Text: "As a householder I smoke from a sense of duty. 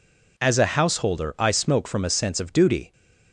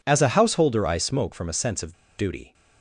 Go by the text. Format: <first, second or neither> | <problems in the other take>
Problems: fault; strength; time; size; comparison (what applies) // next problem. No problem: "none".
first | pauses between "of" and "duty"; slight; at 1.9 s; 0.24 s long